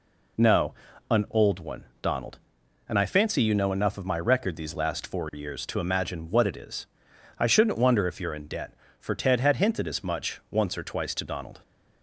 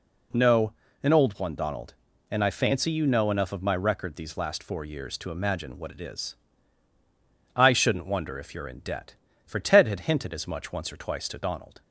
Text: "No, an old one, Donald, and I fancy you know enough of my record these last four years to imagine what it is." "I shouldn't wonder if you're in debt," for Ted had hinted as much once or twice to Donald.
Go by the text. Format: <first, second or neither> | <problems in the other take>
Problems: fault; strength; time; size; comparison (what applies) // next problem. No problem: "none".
neither | none